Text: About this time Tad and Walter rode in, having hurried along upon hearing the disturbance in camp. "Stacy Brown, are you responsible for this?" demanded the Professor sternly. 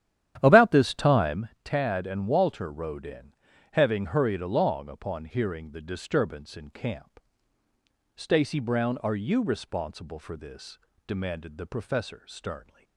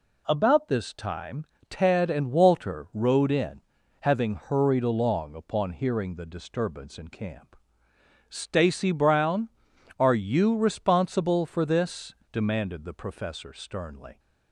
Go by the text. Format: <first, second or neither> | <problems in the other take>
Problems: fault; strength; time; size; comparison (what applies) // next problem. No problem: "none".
second | starts louder than the rest; strong; until 1.5 s; 11 dB // pauses between "time" and "Tad"; slight; at 1.4 s; 0.16 s long; slight in the second